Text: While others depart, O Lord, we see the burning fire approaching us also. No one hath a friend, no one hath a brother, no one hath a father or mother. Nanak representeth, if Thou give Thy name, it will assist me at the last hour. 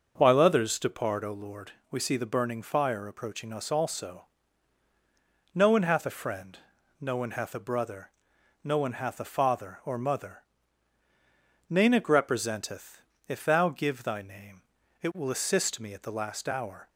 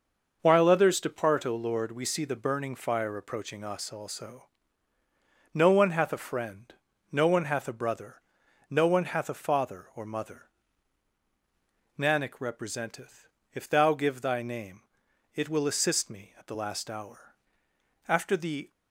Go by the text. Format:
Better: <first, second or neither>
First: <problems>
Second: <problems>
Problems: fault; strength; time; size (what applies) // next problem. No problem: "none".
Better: first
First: none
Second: goes on to say "After the"; noticeable; from 18.0 s on; 0.62 s long